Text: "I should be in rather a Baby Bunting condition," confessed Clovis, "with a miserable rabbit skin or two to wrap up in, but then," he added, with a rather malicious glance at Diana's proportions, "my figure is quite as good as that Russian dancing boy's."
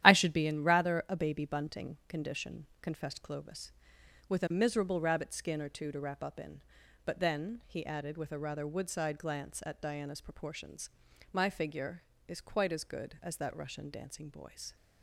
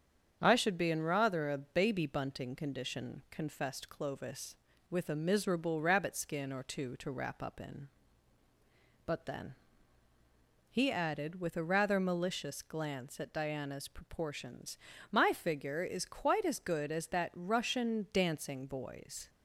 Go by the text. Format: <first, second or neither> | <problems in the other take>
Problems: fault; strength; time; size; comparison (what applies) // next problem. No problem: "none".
second | starts louder than the rest; strong; until 1.0 s; 11.5 dB; strong in the second // says "woodside" for "malicious"; at 8.6 s